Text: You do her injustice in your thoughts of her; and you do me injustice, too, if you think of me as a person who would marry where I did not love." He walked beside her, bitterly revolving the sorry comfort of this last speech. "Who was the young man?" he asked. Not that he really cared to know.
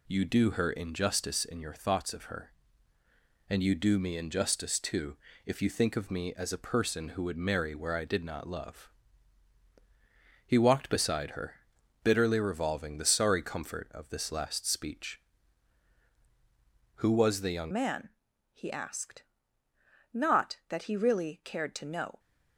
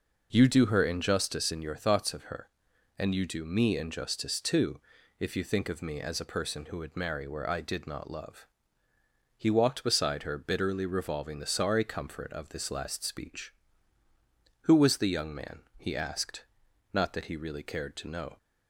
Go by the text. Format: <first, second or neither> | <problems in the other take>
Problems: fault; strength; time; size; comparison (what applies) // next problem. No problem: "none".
second | changes voice at "man"; from 17.7 s on; 4.4 s long